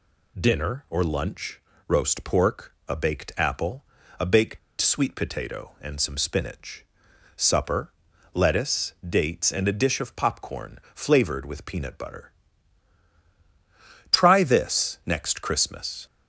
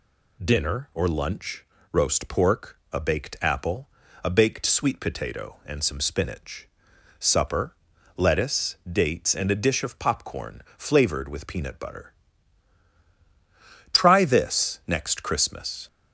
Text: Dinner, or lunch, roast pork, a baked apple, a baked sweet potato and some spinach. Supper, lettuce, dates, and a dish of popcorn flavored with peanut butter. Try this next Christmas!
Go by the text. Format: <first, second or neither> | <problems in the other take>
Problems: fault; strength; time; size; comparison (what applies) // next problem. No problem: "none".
second | pauses between "baked" and "sweet"; slight; at 4.5 s; 0.22 s long // pauses between "popcorn" and "flavored"; slight; at 10.7 s; 0.16 s long; slight in the second